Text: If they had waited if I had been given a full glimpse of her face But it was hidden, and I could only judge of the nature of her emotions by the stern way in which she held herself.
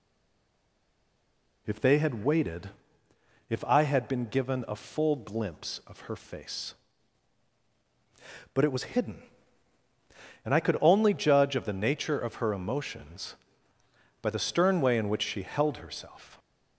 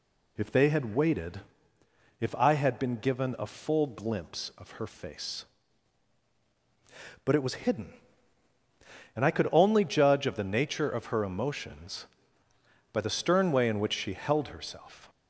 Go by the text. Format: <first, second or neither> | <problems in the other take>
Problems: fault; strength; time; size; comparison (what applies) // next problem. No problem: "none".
second | stays silent before the first word; noticeable; until 1.6 s; 1.6 s long // pauses between "waited" and "if"; noticeable; at 2.7 s; 0.78 s long; noticeable in the second